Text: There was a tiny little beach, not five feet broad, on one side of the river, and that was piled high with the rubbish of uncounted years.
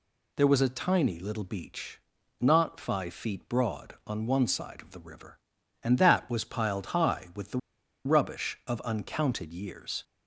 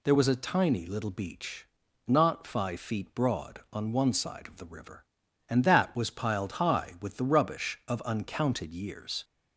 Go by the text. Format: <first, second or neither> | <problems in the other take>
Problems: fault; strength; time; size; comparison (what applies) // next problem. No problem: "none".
second | pauses between "the" and "rubbish"; noticeable; at 7.5 s; 0.47 s long